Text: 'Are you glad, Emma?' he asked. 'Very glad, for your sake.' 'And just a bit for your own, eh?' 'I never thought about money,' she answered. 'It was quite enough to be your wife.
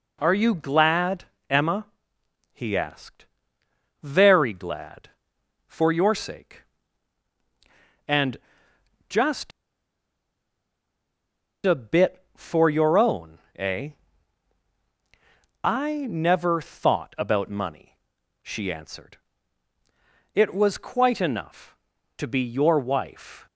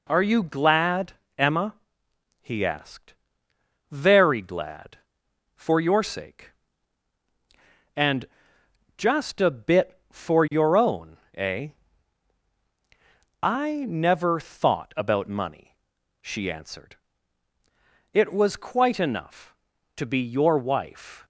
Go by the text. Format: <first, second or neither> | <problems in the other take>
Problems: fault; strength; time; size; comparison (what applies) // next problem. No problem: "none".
second | pauses between "And" and "just"; noticeable; at 8.3 s; 0.70 s long; noticeable in the second // pauses between "just" and "a"; strong; at 9.5 s; 2.1 s long